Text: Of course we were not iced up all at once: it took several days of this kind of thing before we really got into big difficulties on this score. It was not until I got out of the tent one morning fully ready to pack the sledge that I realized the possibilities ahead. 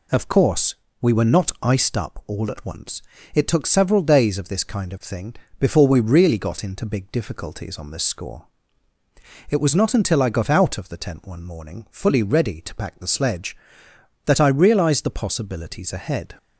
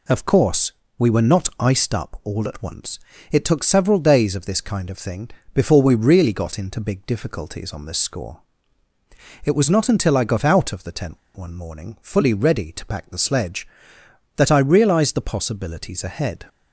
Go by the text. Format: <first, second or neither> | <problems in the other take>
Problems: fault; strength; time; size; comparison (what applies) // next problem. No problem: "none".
first | pauses between "course" and "we"; slight; at 0.7 s; 0.26 s long; slight in the first // pauses between "thing" and "before"; slight; at 5.2 s; 0.22 s long; slight in the first // pauses between "tent" and "one"; slight; at 11.1 s; 0.17 s long